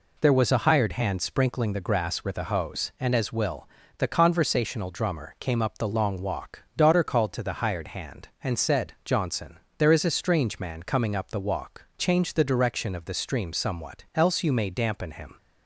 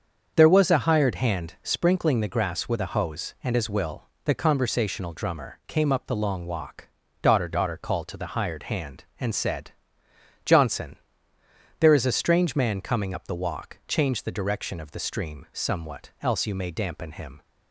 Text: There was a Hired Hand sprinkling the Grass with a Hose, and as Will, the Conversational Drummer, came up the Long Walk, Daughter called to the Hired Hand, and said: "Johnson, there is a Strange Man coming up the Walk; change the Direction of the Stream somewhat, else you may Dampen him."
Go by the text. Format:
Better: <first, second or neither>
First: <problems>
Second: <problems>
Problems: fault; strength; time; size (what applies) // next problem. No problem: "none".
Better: first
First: none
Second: starts louder than the rest; until 1.3 s; 7 dB // says "Daughter" twice; at 7.4 s